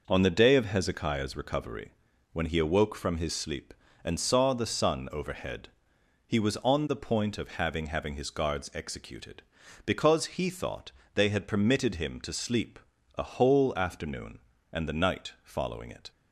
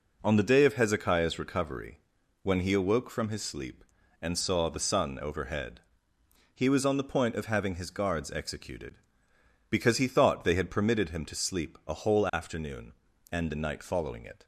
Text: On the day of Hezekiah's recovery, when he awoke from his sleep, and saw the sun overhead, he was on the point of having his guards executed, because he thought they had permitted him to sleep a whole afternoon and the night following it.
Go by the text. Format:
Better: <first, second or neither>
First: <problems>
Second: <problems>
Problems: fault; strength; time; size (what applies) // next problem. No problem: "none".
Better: second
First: says "having" twice; at 7.8 s // pauses between "thought" and "they"; slight; at 10.9 s; 0.22 s long // pauses between "sleep" and "a"; at 12.7 s; 0.38 s long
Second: none